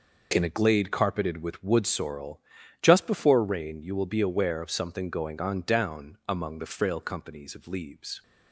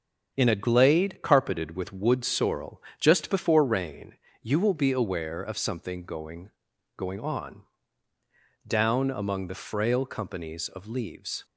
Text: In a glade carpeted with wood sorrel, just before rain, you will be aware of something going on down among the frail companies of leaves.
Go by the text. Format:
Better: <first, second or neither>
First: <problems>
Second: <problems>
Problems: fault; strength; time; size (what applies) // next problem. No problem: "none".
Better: first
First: none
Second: starts louder than the rest; until 1.3 s; 6.5 dB // says "going" twice; at 6.9 s // pauses between "on" and "down"; at 7.6 s; 1.0 s long